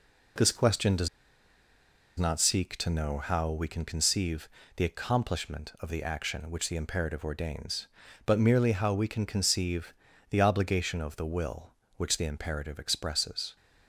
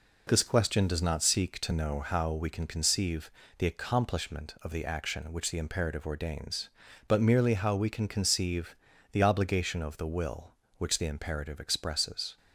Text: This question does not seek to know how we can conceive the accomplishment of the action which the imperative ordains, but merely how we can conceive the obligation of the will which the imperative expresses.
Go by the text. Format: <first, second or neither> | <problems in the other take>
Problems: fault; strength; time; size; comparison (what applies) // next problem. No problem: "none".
second | pauses between "does" and "not"; at 1.0 s; 1.0 s long // pauses between "conceive" and "the"; slight; at 4.4 s; 0.28 s long; slight in the second // pauses between "conceive" and "the"; at 9.9 s; 0.38 s long; also in the second